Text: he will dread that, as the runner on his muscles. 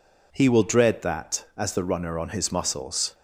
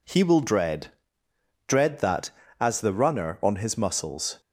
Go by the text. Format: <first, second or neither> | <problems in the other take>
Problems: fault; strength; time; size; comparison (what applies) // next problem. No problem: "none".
first | says "dread" twice; at 1.6 s